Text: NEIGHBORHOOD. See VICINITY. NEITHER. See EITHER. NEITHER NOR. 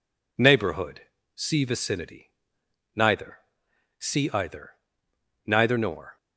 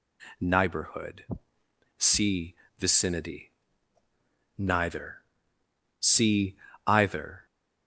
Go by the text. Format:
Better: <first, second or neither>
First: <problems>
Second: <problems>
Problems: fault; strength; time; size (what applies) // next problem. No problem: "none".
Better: first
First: none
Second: pauses between "See" and "VICINITY"; slight; at 2.5 s; 0.24 s long // pauses between "See" and "EITHER"; slight; at 6.5 s; 0.27 s long // stops before "NEITHER NOR"; at 7.4 s